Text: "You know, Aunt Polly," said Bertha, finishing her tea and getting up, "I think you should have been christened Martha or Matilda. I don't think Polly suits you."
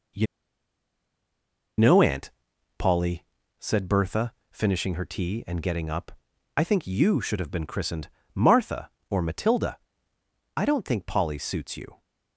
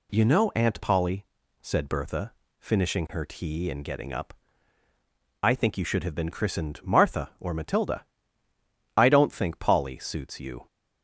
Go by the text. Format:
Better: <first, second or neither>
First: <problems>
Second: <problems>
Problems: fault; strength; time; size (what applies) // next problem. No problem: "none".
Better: second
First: pauses between "You" and "know"; strong; at 0.2 s; 1.5 s long // pauses between "Aunt" and "Polly"; noticeable; at 2.2 s; 0.48 s long // pauses between "christened" and "Martha"; slight; at 8.0 s; 0.28 s long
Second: none